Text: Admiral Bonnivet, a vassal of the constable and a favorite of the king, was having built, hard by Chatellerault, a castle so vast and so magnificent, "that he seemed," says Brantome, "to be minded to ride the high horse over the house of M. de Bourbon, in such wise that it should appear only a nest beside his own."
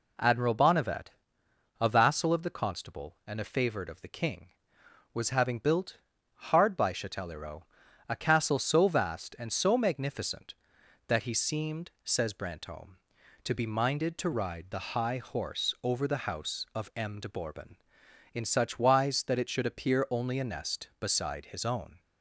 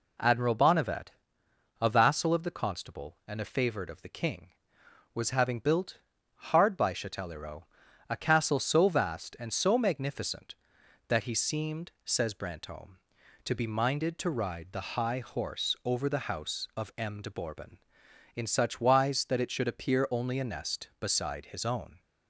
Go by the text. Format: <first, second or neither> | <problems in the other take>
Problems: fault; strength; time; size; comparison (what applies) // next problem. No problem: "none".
neither | none